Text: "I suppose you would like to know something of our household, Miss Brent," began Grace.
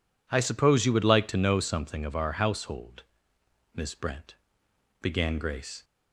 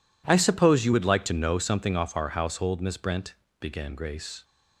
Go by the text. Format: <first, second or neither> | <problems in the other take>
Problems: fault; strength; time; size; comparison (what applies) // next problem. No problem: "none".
first | says "off" for "of"; at 1.9 s